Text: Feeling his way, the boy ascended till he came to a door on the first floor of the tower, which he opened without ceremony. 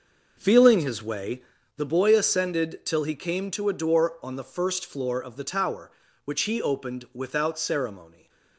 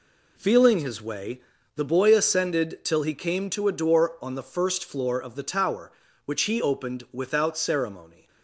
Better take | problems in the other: second | starts louder than the rest; noticeable; until 1.6 s; 6 dB // stays silent after the last word; slight; from 8.0 s on; 0.5 s long

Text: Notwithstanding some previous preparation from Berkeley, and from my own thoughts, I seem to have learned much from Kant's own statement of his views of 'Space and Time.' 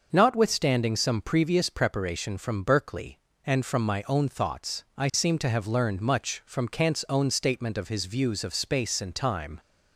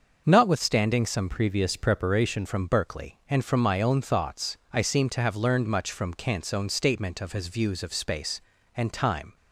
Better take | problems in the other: first | starts louder than the rest; until 1.2 s; 6.5 dB // changes voice from "previous" to "preparation"; from 1.3 to 2.4 s; 1.1 s long

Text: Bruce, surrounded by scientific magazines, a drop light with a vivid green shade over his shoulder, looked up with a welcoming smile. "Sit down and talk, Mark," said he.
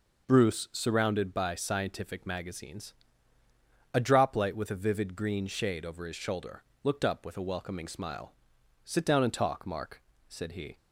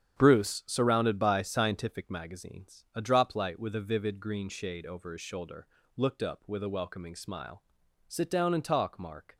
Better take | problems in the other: first | starts louder than the rest; strong; until 1.2 s; 8.5 dB // stops before "said he"; at 9.3 s

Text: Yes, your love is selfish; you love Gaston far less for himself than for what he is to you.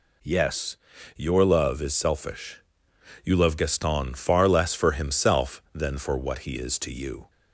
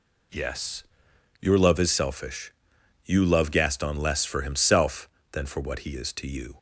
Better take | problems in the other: first | skips "far"; at 3.9 s

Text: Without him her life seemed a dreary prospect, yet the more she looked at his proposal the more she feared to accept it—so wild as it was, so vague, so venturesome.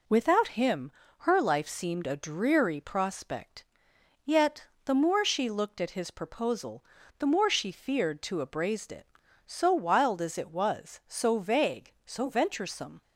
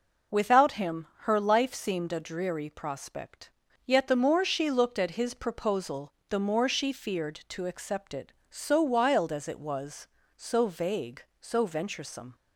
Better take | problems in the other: second | pauses between "him" and "her"; slight; at 0.9 s; 0.28 s long // pauses between "yet" and "the"; slight; at 4.6 s; 0.18 s long // pauses between "proposal" and "the"; slight; at 6.8 s; 0.34 s long; slight in the second // says "abrased" for "accept"; at 8.4 s

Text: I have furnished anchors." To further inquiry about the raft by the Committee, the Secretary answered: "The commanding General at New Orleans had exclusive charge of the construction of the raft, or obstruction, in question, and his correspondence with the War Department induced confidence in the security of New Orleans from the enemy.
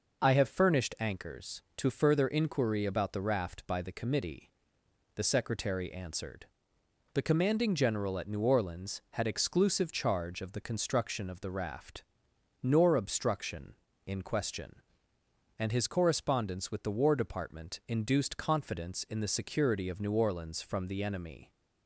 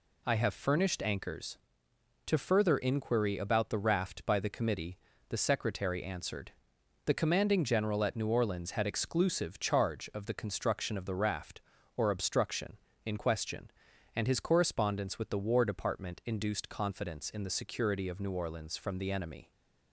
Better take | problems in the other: second | says "nor" for "or"; at 12.6 s

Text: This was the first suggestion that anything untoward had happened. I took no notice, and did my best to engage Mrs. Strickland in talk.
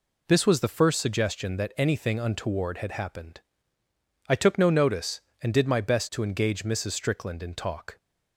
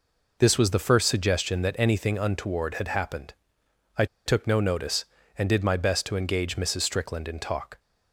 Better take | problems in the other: first | pauses between "I" and "took"; slight; at 4.0 s; 0.20 s long

